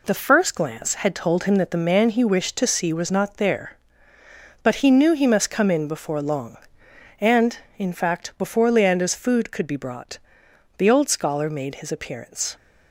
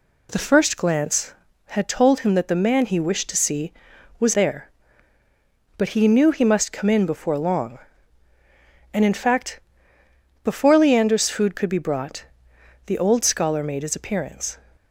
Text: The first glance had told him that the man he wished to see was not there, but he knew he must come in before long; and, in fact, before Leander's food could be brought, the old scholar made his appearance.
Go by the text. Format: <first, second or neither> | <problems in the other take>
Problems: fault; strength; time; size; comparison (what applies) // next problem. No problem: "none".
first | skips "not"; at 4.3 s